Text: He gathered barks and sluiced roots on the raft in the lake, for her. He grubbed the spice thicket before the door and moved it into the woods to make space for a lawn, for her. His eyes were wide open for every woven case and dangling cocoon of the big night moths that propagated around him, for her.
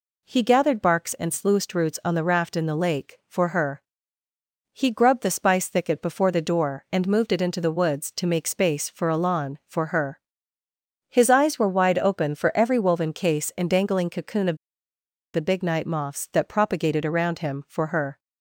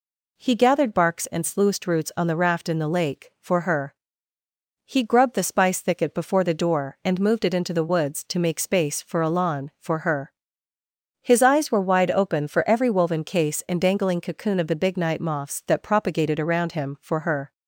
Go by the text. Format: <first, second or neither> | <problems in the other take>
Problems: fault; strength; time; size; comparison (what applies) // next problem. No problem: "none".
second | pauses between "of" and "the"; noticeable; at 14.5 s; 0.77 s long